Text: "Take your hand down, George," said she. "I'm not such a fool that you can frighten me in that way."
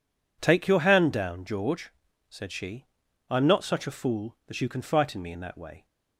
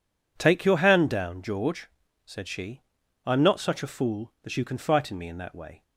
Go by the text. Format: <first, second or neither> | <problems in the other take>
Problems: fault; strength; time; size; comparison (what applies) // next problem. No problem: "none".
neither | none